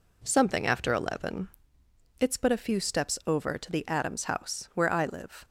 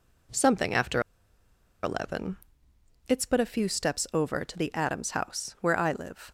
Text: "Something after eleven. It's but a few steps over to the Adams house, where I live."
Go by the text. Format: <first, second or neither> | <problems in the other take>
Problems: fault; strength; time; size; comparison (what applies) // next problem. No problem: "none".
first | pauses between "after" and "eleven"; noticeable; at 0.9 s; 0.83 s long